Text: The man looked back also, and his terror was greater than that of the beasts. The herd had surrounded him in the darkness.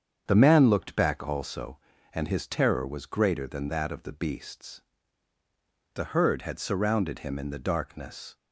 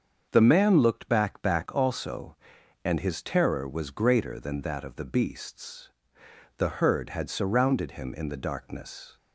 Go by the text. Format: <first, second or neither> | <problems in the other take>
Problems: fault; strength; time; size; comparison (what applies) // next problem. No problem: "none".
first | starts louder than the rest; until 1.3 s; 6.5 dB; strong in the first // says "back" twice; at 1.4 s